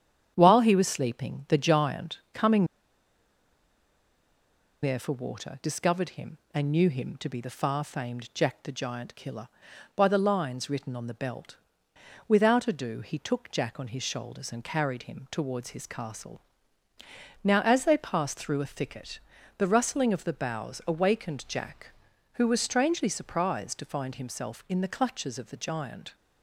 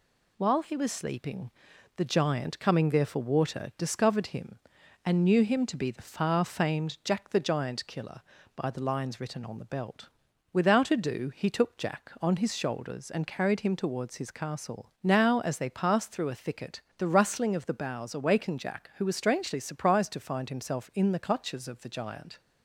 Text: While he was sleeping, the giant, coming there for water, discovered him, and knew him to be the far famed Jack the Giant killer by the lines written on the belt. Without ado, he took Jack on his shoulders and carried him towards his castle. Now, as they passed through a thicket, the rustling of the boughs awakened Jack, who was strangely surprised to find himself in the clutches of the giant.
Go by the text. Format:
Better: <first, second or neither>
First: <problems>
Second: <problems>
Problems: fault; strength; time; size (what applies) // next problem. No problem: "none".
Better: second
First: starts louder than the rest; strong; until 1.3 s; 8.5 dB // pauses between "coming" and "there"; strong; at 2.6 s; 2.1 s long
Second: none